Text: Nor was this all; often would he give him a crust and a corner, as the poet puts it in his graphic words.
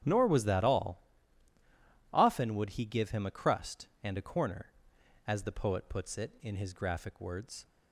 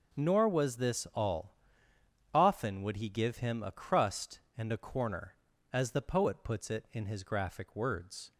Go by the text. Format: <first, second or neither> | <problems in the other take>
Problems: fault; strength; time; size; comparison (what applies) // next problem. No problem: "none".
second | starts louder than the rest; strong; until 2.1 s; 9.5 dB; noticeable in the second // says "that" for "this"; at 0.4 s